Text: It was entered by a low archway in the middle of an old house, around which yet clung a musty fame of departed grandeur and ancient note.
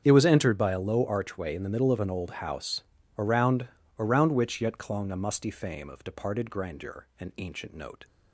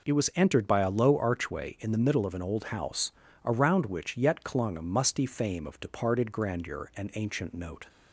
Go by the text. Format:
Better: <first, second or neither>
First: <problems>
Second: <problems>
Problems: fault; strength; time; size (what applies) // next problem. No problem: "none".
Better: second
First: starts louder than the rest; strong; until 1.0 s; 7.5 dB // says "around" twice; at 3.9 s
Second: none